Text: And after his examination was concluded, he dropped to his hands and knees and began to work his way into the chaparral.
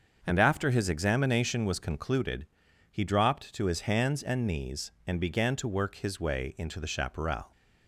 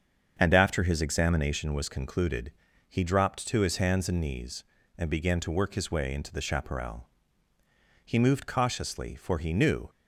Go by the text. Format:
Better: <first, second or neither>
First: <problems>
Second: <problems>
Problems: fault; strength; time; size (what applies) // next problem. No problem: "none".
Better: first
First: starts louder than the rest; until 1.2 s; 6.5 dB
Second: starts louder than the rest; strong; until 1.4 s; 7.5 dB // goes on to say "He moved cautiously for he knew"; strong; from 8.0 s on; 1.8 s long